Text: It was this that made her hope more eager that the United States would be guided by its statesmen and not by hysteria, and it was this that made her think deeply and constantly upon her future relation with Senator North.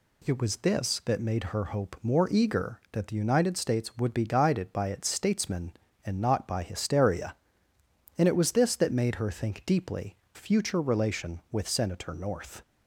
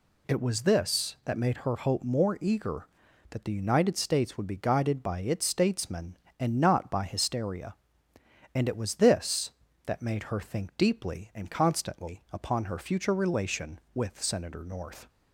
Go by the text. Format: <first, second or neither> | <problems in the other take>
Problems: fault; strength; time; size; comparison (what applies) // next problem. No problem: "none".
second | skips "and constantly upon her"; at 10.2 s